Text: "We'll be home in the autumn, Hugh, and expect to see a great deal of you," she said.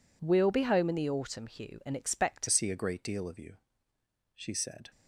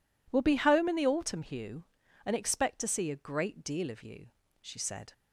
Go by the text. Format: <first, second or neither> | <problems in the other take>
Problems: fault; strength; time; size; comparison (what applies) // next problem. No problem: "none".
second | changes voice at "see"; from 2.4 s on; 2.4 s long